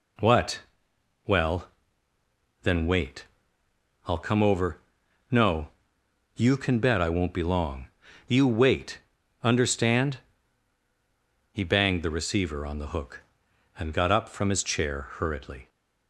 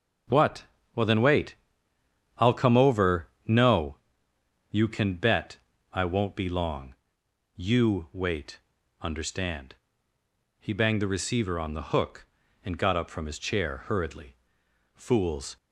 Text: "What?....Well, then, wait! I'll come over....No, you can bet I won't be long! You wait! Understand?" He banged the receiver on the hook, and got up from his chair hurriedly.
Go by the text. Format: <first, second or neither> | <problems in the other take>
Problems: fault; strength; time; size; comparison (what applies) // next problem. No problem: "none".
first | pauses between "bet" and "I"; slight; at 5.5 s; 0.34 s long // goes on to say "Fools"; noticeable; from 14.9 s on; 0.62 s long